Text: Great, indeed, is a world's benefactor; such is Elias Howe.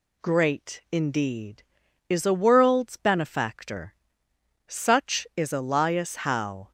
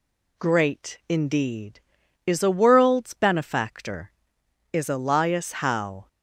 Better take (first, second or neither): first